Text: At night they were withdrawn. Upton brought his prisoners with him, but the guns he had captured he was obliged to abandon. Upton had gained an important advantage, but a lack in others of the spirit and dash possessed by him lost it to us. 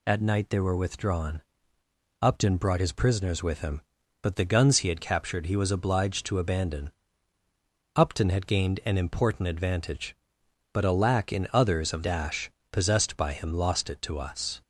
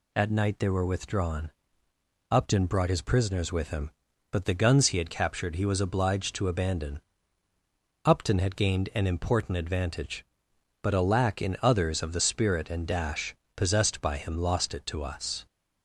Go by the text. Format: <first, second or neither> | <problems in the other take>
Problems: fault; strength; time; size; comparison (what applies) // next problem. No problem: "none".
second | skips "the spirit and"; at 12.0 s // pauses between "dash" and "possessed"; slight; at 12.4 s; 0.22 s long; slight in the second